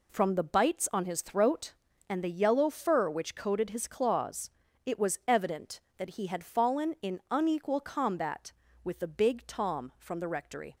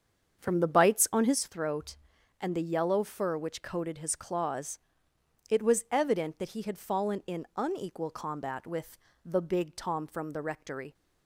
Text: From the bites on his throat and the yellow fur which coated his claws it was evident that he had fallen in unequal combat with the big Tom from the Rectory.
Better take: first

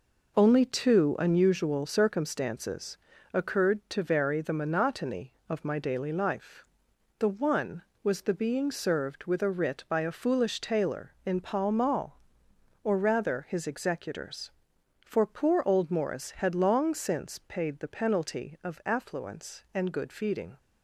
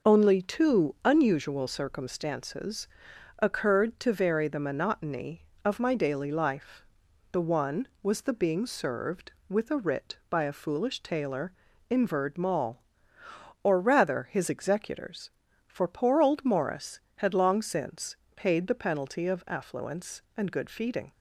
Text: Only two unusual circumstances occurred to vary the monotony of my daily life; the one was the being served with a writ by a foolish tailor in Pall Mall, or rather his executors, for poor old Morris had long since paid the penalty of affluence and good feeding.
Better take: first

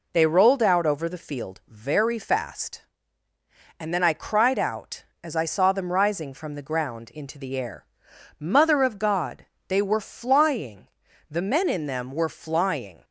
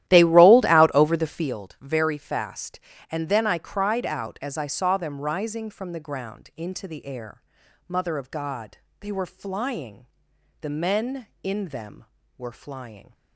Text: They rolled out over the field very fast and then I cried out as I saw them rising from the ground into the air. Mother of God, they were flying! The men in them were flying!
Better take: first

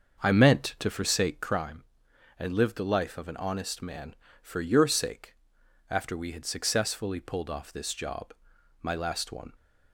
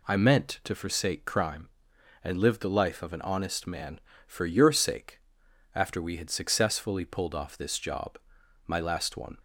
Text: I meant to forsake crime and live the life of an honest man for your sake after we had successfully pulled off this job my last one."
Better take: second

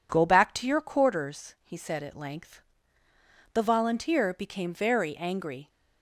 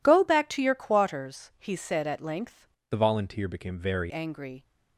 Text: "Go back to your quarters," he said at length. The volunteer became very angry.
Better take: first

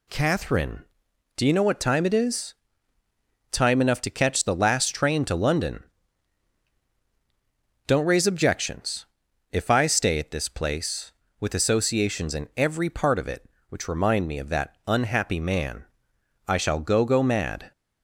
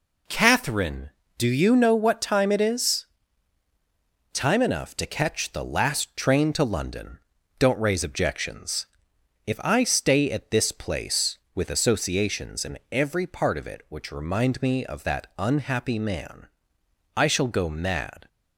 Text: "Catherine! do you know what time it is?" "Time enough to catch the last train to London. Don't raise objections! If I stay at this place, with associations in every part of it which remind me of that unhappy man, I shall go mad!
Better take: second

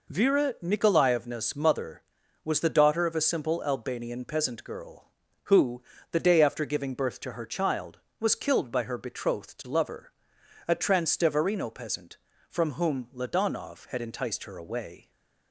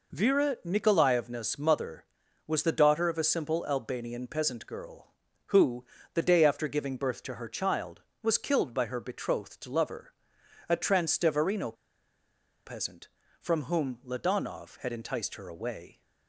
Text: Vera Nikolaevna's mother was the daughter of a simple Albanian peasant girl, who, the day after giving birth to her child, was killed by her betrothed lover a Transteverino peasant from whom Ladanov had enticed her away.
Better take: first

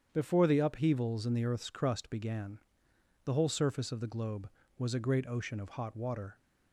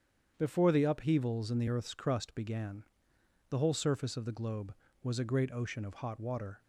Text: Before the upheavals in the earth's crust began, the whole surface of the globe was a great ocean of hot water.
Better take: neither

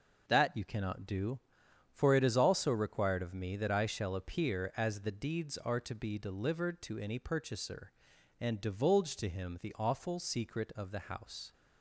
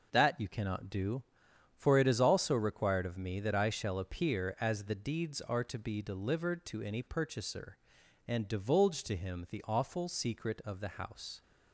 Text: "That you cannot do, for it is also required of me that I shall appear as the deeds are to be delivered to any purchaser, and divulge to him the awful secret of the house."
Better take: neither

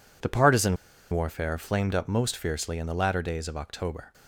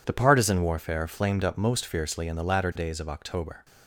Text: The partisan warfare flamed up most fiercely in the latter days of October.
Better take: second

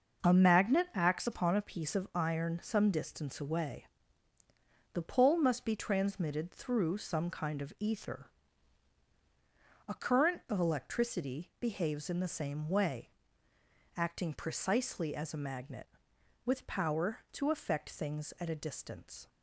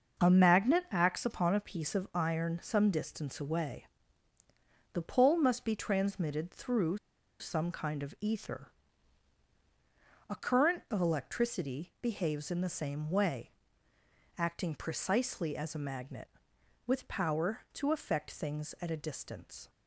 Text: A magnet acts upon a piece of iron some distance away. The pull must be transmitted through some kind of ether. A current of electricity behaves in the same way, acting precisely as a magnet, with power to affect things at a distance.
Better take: first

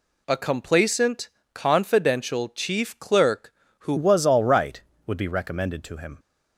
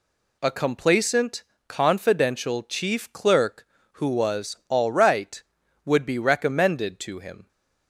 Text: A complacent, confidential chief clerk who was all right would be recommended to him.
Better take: second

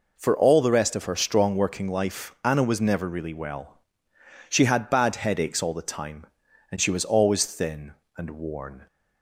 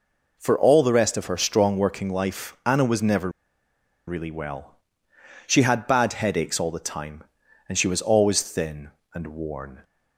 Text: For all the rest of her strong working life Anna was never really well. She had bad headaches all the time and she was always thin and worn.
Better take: first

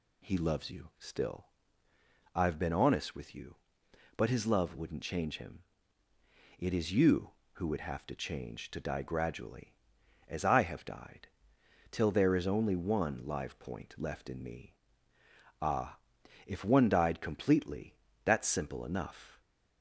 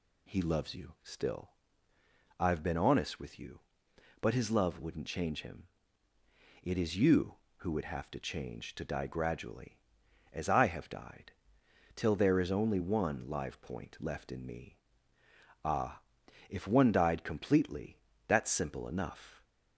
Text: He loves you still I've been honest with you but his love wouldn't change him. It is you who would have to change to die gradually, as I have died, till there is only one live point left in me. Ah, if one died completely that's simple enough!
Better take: neither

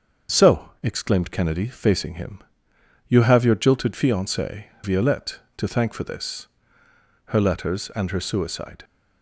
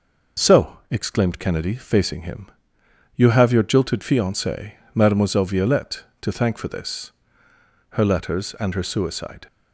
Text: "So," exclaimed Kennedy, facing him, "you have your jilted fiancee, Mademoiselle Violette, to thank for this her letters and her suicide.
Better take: second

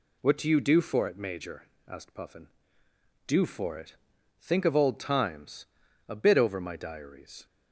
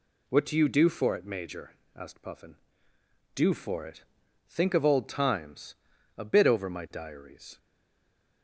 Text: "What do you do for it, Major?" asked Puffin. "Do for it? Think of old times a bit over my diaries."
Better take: first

